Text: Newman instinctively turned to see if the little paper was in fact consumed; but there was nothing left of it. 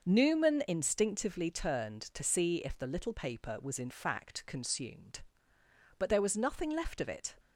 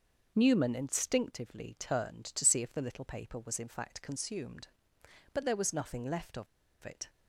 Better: first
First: starts louder than the rest; noticeable; until 1.0 s; 6 dB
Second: starts louder than the rest; noticeable; until 1.3 s; 6 dB // pauses between "of" and "it"; at 6.4 s; 0.37 s long

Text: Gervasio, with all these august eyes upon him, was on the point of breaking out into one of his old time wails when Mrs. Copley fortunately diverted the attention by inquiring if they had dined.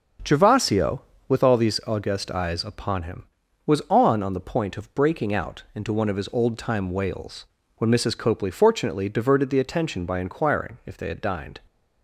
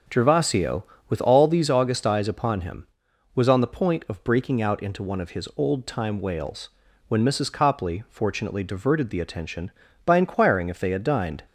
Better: second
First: starts louder than the rest; until 1.5 s; 6.5 dB // says "on" twice; at 4.2 s // pauses between "wails" and "when"; slight; at 7.4 s; 0.30 s long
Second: starts louder than the rest; until 1.3 s; 6.5 dB // pauses between "wails" and "when"; at 6.6 s; 0.38 s long

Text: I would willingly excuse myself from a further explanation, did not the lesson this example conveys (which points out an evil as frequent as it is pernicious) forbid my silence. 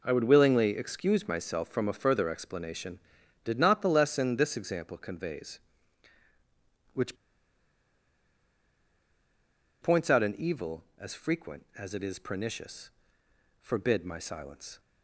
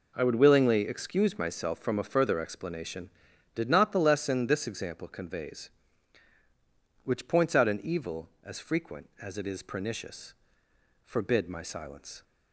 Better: second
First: pauses between "which" and "points"; strong; at 7.1 s; 2.6 s long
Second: none

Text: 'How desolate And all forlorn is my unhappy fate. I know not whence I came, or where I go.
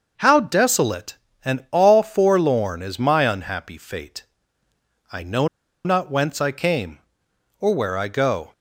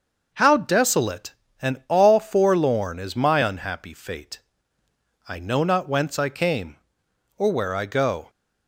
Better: second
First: starts louder than the rest; noticeable; until 1.1 s; 6 dB // pauses between "know" and "not"; at 5.4 s; 0.37 s long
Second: starts louder than the rest; noticeable; until 1.3 s; 6 dB

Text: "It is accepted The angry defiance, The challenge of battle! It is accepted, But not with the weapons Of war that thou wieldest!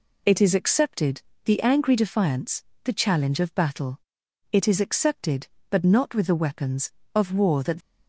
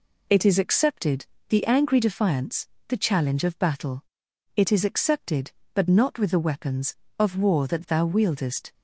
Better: second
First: pauses between "accepted" and "The"; slight; at 1.2 s; 0.22 s long // stops before "thou wieldest"; at 7.8 s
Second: pauses between "accepted" and "The"; slight; at 1.2 s; 0.22 s long

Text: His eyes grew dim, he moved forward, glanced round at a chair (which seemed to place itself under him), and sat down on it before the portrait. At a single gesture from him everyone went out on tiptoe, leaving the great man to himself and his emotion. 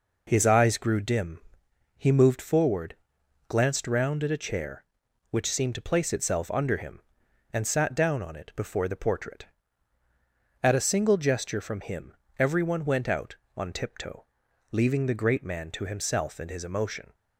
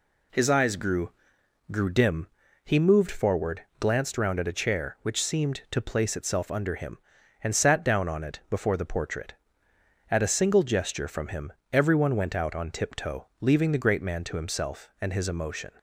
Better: first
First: pauses between "him" and "everyone"; slight; at 12.1 s; 0.26 s long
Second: says "grew" twice; at 1.7 s // pauses between "him" and "everyone"; slight; at 11.5 s; 0.20 s long

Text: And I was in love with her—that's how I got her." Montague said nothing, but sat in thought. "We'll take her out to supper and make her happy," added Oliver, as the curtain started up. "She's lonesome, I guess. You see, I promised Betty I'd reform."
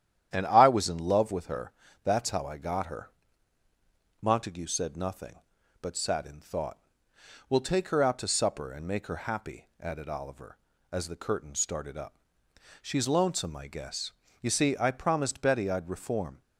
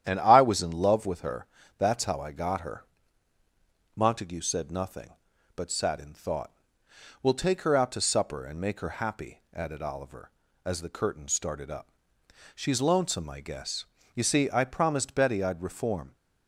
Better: neither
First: starts louder than the rest; strong; until 1.3 s; 10.5 dB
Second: starts louder than the rest; strong; until 1.0 s; 10.5 dB

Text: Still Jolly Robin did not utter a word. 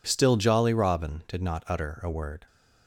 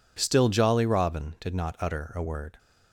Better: neither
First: none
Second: none

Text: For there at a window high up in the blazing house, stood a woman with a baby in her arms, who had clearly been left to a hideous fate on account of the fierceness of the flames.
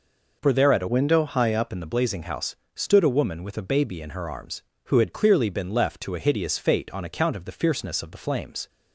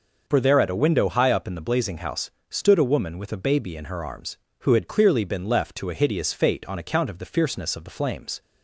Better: second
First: changes voice from "window" to "up"; from 0.8 to 1.6 s; 0.8 s long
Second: none

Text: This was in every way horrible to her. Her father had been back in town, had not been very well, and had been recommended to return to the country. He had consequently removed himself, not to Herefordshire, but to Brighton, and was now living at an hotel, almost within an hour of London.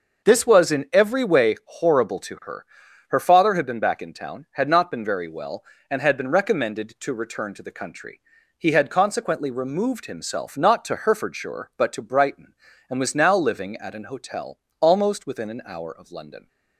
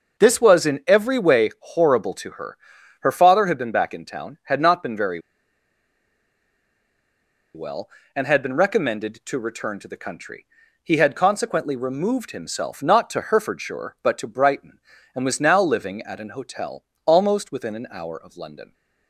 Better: first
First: starts louder than the rest; until 1.3 s; 6 dB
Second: starts louder than the rest; noticeable; until 1.2 s; 6 dB // pauses between "very" and "well"; strong; at 5.1 s; 2.3 s long

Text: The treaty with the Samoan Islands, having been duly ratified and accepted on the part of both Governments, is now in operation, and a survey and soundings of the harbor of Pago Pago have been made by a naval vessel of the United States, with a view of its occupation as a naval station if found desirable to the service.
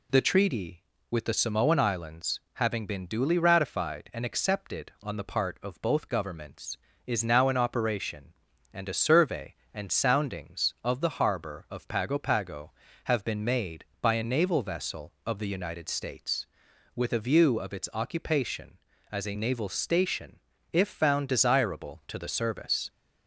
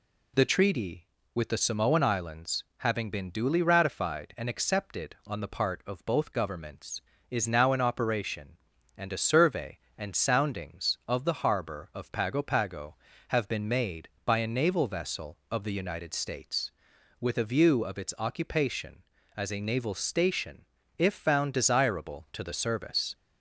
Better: neither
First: pauses between "station" and "if"; slight; at 20.3 s; 0.34 s long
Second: pauses between "station" and "if"; slight; at 20.6 s; 0.34 s long

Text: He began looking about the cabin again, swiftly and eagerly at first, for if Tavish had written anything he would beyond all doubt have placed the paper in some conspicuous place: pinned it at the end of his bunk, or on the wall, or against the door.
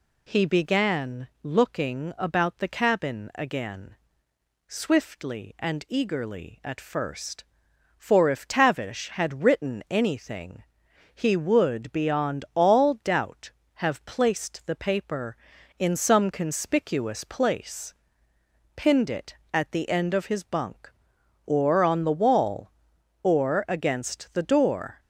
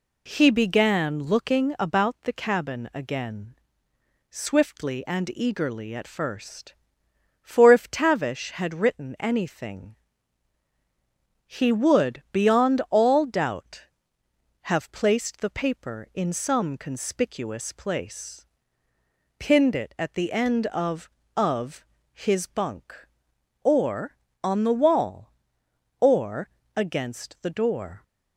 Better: first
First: pauses between "anything" and "he"; noticeable; at 10.6 s; 0.52 s long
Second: pauses between "anything" and "he"; strong; at 9.9 s; 1.5 s long // says "of" twice; at 21.3 s // pauses between "or" and "against"; slight; at 26.4 s; 0.26 s long

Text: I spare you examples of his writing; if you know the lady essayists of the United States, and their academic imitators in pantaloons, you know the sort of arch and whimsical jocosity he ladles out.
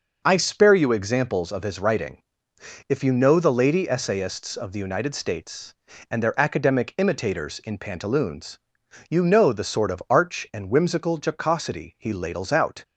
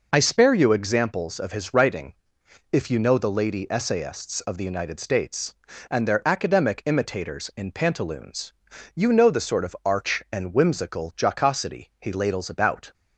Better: first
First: none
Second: says "about" for "out"; at 12.4 s

